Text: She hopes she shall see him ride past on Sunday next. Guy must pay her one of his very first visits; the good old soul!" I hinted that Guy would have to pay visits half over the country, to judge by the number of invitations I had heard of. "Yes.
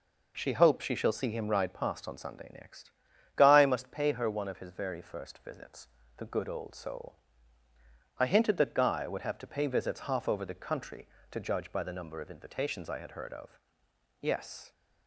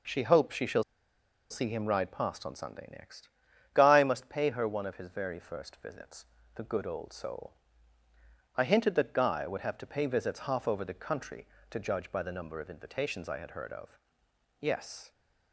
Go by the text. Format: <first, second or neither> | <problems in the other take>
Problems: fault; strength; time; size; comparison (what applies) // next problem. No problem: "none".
first | pauses between "shall" and "see"; noticeable; at 0.8 s; 0.67 s long